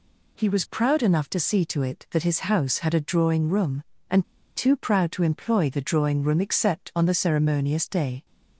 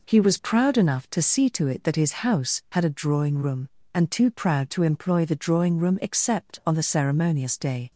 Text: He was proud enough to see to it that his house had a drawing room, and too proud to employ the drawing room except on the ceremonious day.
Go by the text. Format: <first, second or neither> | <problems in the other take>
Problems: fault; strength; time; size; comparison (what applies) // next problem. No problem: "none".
second | pauses between "and" and "too"; slight; at 4.2 s; 0.33 s long